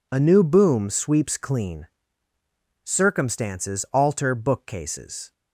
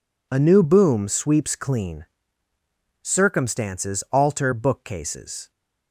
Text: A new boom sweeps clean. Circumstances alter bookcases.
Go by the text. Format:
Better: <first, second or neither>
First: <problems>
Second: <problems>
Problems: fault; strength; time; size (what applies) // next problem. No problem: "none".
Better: neither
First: none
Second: none